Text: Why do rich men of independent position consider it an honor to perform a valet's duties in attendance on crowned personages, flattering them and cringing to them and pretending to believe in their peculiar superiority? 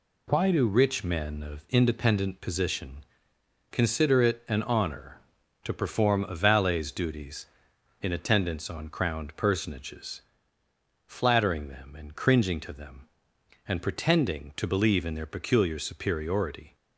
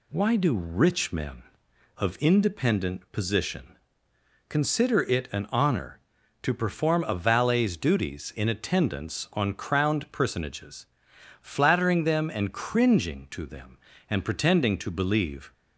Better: first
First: pauses between "position" and "consider"; noticeable; at 3.0 s; 0.68 s long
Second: pauses between "position" and "consider"; noticeable; at 3.7 s; 0.70 s long // stops before "in their peculiar superiority"; at 15.5 s

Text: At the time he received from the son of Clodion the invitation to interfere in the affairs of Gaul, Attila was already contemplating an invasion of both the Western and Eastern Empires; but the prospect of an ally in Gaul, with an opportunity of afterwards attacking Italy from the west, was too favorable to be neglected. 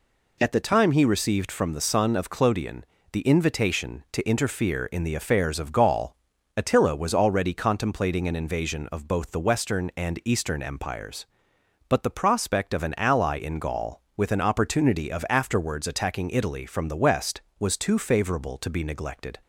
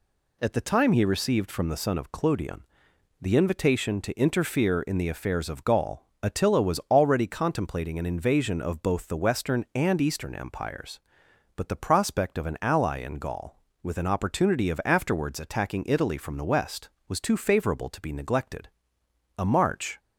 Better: first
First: pauses between "Clodion" and "the"; slight; at 2.8 s; 0.26 s long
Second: pauses between "Clodion" and "the"; noticeable; at 2.6 s; 0.58 s long // goes on to say "A march"; noticeable; from 19.3 s on; 0.62 s long

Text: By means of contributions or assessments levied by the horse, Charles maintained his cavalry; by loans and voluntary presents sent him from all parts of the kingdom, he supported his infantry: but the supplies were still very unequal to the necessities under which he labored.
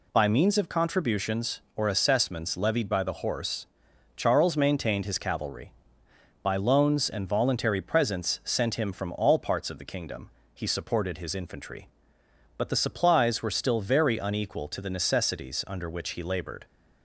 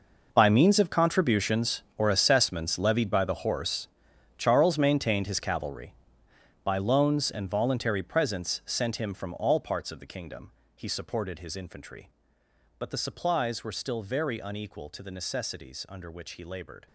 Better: first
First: none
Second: gets quieter; strong; throughout; 15 dB

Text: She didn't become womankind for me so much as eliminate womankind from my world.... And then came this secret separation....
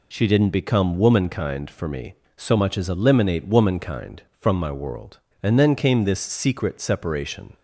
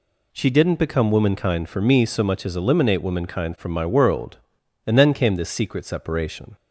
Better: neither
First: none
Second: none

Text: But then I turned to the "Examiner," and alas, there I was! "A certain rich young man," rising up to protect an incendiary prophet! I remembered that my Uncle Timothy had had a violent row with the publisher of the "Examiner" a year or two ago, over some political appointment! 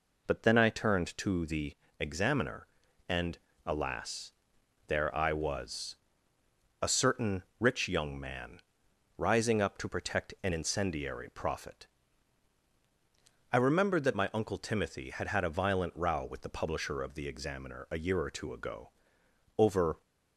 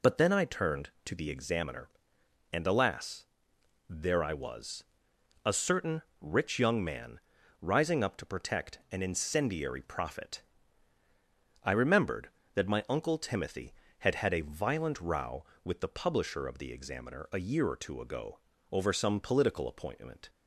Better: second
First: pauses between "the" and "Examiner"; slight; at 1.7 s; 0.24 s long // pauses between "and" and "alas"; slight; at 3.3 s; 0.28 s long // pauses between "certain" and "rich"; slight; at 7.4 s; 0.16 s long // stops before "some political appointment"; at 20.0 s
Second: pauses between "certain" and "rich"; slight; at 6.0 s; 0.18 s long

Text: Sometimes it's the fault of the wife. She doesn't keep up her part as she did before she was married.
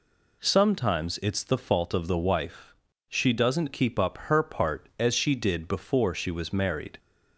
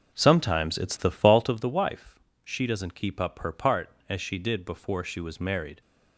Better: first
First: none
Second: starts louder than the rest; noticeable; until 1.6 s; 5.5 dB

